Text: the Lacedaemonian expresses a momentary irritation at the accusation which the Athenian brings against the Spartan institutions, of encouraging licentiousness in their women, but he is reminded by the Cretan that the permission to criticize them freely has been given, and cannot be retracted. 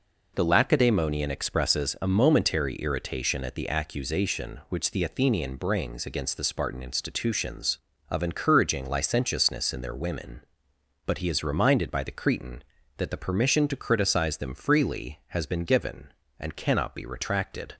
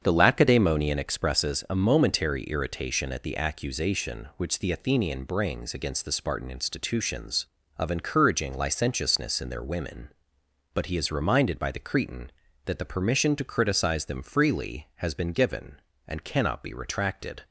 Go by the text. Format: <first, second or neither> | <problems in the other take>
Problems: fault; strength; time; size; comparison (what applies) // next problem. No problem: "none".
first | starts louder than the rest; strong; until 1.2 s; 7.5 dB